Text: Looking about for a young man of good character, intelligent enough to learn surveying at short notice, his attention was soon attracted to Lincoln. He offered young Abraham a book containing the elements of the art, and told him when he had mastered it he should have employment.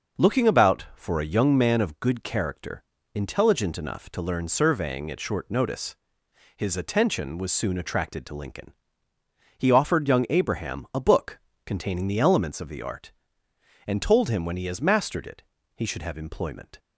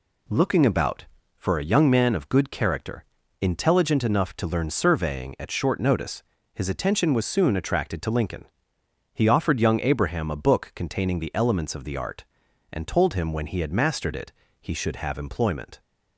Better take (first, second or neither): second